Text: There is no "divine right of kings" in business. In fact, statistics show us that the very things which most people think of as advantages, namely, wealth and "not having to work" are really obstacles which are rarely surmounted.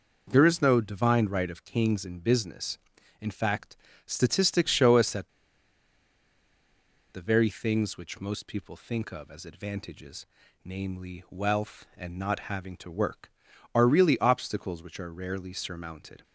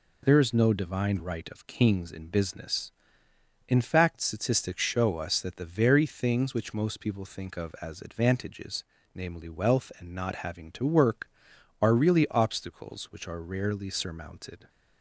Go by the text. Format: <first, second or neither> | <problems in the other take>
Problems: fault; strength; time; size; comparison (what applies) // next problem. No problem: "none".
second | pauses between "that" and "the"; strong; at 5.2 s; 1.8 s long